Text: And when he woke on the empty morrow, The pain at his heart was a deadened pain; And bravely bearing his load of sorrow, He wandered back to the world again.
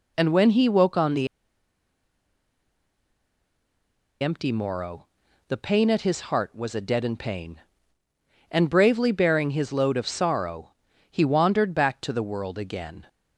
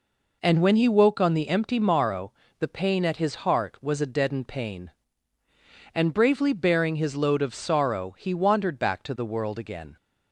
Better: second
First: pauses between "the" and "empty"; strong; at 1.2 s; 2.9 s long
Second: none

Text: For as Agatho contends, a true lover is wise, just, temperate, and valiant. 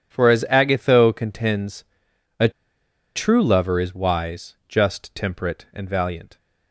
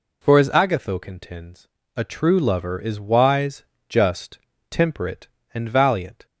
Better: second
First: pauses between "a" and "true"; noticeable; at 2.4 s; 0.66 s long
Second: none

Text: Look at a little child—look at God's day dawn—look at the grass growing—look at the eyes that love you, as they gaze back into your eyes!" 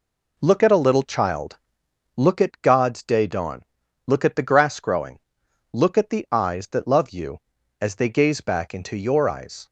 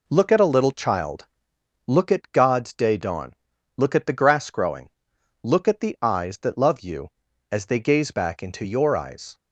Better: neither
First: none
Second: none

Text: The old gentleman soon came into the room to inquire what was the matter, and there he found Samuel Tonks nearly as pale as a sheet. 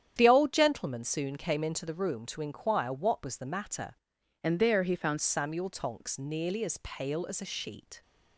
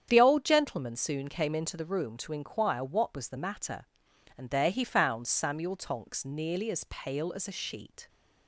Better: second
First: starts louder than the rest; strong; until 1.1 s; 9.5 dB // changes voice from "and" to "found"; from 4.4 to 5.1 s; 0.7 s long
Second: starts louder than the rest; strong; until 1.1 s; 8.5 dB

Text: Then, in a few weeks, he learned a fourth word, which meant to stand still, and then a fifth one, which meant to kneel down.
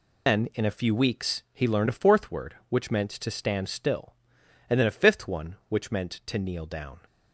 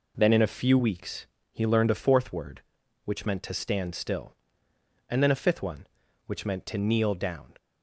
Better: second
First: loses the start of "Then"; at 0.2 s; 120 ms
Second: none

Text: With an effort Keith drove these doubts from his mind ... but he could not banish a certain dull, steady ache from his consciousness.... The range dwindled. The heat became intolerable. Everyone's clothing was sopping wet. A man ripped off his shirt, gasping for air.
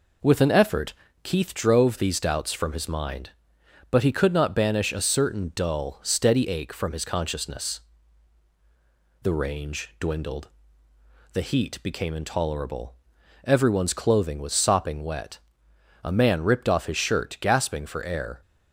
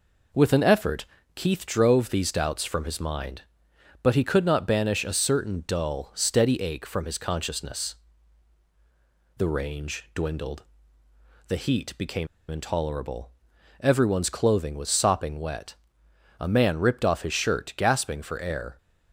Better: first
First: pauses between "effort" and "Keith"; slight; at 0.9 s; 0.30 s long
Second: pauses between "effort" and "Keith"; slight; at 1.0 s; 0.30 s long // pauses between "became" and "intolerable"; slight; at 12.2 s; 0.24 s long

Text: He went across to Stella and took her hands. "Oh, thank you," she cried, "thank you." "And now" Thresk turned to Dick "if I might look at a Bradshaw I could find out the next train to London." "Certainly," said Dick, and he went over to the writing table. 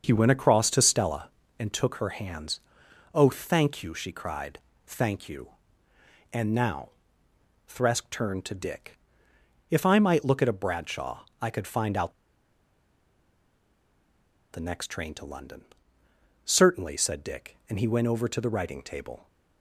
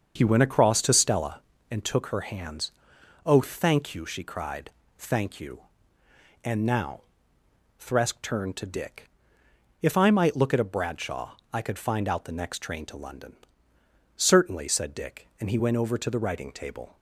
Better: second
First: starts louder than the rest; until 1.0 s; 7 dB // pauses between "now" and "Thresk"; noticeable; at 6.9 s; 0.76 s long // pauses between "Dick" and "if"; noticeable; at 8.9 s; 0.72 s long // pauses between "Bradshaw" and "I"; slight; at 11.2 s; 0.16 s long // pauses between "out" and "the"; strong; at 12.1 s; 2.4 s long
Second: starts louder than the rest; until 1.1 s; 7 dB // pauses between "now" and "Thresk"; noticeable; at 7.0 s; 0.76 s long // pauses between "Dick" and "if"; noticeable; at 9.1 s; 0.72 s long // pauses between "Bradshaw" and "I"; slight; at 11.3 s; 0.16 s long

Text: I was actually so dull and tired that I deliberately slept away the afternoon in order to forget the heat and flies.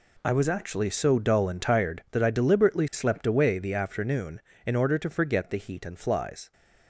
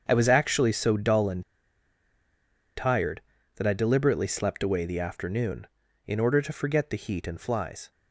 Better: first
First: none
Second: starts louder than the rest; strong; until 1.0 s; 7.5 dB // pauses between "and" and "tired"; strong; at 1.4 s; 1.3 s long

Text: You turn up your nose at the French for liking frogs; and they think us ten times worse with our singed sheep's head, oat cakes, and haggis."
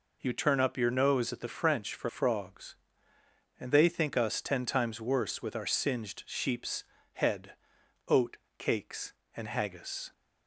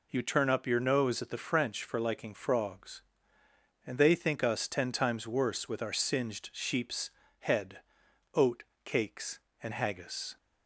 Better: second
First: skips "liking"; at 2.0 s // pauses between "sheep's" and "head"; slight; at 6.8 s; 0.30 s long // pauses between "oat" and "cakes"; slight; at 8.3 s; 0.22 s long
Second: pauses between "sheep's" and "head"; slight; at 7.1 s; 0.30 s long // pauses between "oat" and "cakes"; slight; at 8.6 s; 0.22 s long

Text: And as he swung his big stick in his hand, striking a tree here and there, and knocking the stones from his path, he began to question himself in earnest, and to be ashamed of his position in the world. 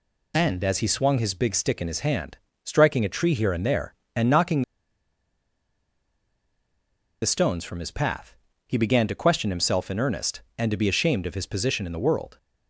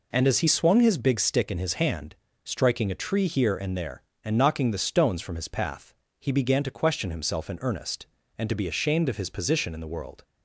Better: second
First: pauses between "knocking" and "the"; strong; at 4.6 s; 2.5 s long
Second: none

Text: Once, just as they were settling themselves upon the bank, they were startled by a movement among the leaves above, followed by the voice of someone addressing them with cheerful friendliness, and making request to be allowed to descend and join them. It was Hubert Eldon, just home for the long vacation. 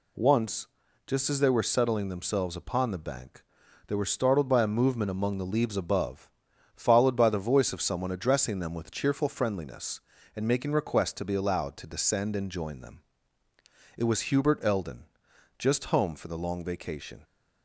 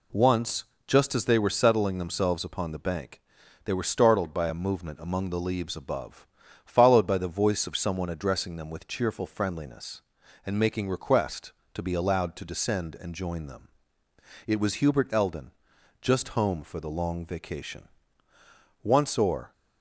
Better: first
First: none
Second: goes on to say "Once or"; noticeable; from 18.8 s on; 0.70 s long

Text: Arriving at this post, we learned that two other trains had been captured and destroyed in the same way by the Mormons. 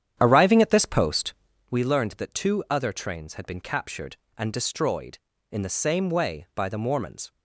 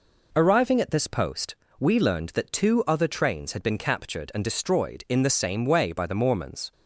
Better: second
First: starts louder than the rest; strong; until 1.7 s; 9.5 dB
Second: none

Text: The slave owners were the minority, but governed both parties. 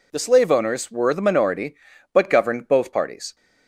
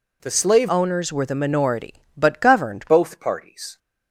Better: first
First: none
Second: changes voice from "owners" to "governed"; from 0.6 to 2.8 s; 2.2 s long

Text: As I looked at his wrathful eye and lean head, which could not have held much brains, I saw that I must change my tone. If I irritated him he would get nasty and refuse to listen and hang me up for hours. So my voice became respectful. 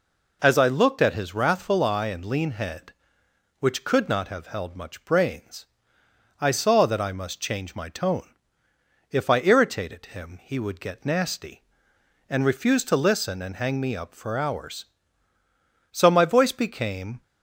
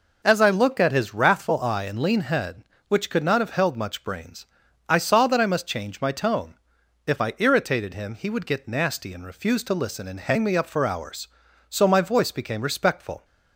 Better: second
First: stops before "respectful"; at 17.2 s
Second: none

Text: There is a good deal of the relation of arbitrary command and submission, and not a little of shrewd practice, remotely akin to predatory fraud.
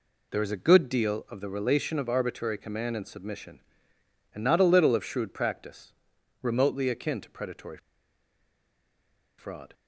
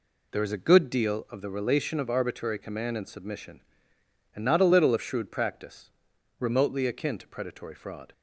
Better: second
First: pauses between "predatory" and "fraud"; strong; at 7.7 s; 1.6 s long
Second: none

